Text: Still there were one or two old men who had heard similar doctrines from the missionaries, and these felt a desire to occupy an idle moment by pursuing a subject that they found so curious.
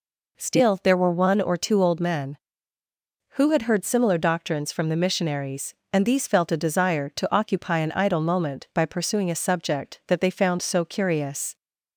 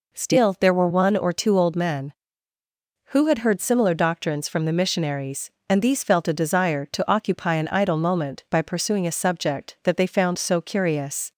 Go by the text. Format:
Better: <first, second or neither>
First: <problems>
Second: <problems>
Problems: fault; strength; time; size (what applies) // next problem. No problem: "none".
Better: neither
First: none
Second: none